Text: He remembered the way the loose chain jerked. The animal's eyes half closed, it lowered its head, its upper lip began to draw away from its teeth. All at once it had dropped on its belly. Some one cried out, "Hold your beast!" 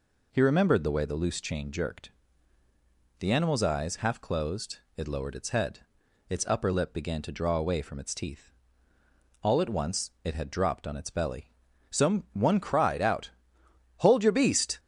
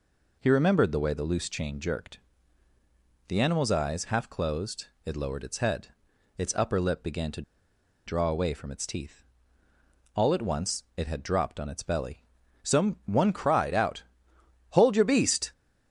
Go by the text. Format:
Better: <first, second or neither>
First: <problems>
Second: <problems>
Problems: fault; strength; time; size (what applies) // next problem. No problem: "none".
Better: first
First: none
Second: pauses between "to" and "draw"; noticeable; at 7.4 s; 0.65 s long